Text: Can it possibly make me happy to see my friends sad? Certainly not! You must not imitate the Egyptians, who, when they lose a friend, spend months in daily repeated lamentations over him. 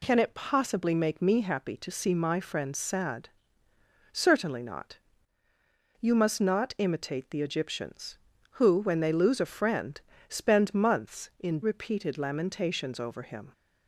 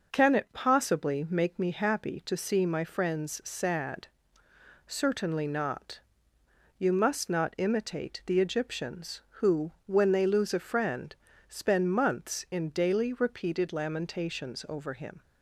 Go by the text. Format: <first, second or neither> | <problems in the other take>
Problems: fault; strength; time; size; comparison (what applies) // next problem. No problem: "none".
second | skips "daily"; at 11.6 s